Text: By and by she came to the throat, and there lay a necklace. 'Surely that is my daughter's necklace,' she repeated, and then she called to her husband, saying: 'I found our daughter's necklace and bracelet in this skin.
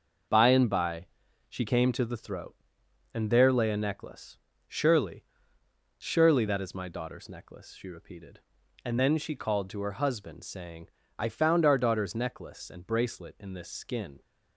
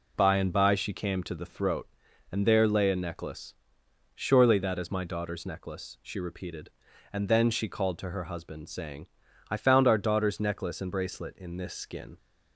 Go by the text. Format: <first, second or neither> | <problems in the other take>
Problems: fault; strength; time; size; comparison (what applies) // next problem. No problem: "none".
second | starts louder than the rest; noticeable; until 1.7 s; 6 dB // pauses between "by" and "she"; at 1.0 s; 0.42 s long // says "Surely" twice; at 5.9 s